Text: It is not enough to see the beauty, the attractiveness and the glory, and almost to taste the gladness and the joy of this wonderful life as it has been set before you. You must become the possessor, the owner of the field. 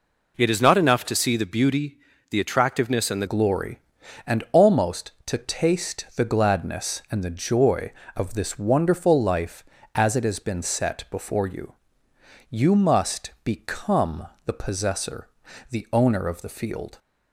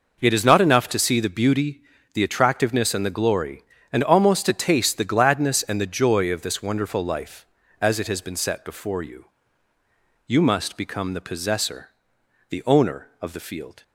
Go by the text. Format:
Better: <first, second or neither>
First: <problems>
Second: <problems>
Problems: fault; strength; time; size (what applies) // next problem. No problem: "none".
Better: second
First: changes voice at "glory"; from 3.2 s on; 13.7 s long // pauses between "become" and "the"; slight; at 14.2 s; 0.18 s long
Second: none